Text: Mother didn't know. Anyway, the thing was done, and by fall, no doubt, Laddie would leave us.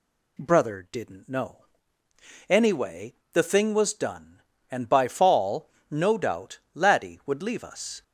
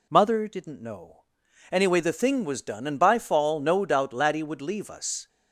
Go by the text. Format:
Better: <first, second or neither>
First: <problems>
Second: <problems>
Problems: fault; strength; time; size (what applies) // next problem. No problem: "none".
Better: second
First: says "Brother" for "Mother"; at 0.3 s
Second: none